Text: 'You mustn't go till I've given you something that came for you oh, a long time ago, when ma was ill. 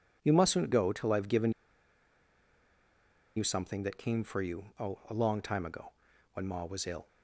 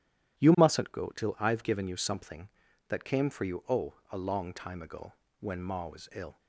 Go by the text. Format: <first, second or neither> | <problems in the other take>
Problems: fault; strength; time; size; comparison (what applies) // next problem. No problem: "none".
second | pauses between "given" and "you"; strong; at 1.5 s; 1.8 s long